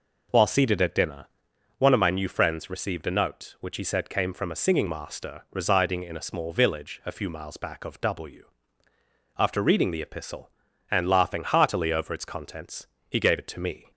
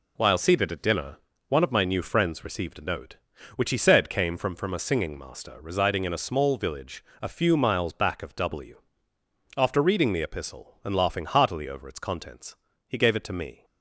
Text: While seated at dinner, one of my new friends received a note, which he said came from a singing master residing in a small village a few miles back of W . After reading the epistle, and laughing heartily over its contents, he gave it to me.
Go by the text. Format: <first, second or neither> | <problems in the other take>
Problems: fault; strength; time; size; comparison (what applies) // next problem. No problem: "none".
first | says "from" twice; at 4.5 s // pauses between "village" and "a"; slight; at 7.0 s; 0.18 s long